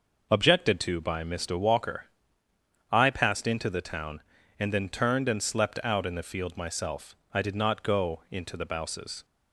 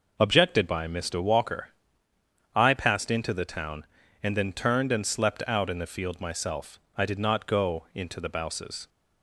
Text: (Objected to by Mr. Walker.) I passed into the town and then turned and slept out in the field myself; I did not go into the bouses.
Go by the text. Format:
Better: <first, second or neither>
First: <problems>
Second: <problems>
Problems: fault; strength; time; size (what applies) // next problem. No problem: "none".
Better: first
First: none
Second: skips "to"; at 0.6 s